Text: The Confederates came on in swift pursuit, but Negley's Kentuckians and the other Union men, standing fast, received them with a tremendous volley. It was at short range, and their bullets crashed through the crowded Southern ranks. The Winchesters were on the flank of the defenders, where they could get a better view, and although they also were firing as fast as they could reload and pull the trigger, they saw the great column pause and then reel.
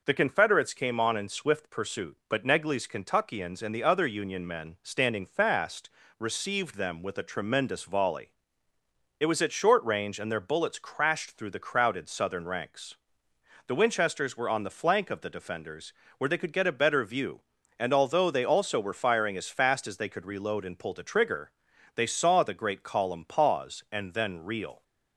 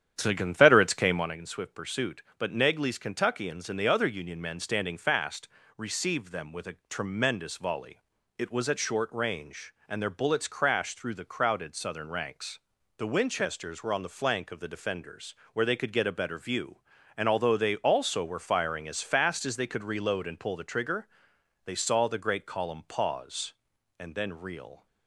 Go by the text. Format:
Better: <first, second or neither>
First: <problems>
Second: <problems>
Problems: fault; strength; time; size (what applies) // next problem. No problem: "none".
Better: first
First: none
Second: starts louder than the rest; strong; until 1.4 s; 9.5 dB